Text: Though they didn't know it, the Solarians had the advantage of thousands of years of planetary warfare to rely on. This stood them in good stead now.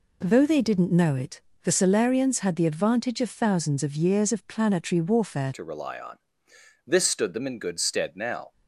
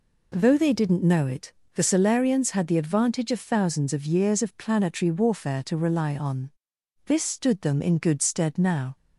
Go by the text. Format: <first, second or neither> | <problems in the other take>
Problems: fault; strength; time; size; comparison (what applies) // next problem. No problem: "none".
second | changes voice at "to"; from 5.5 s on; 3.0 s long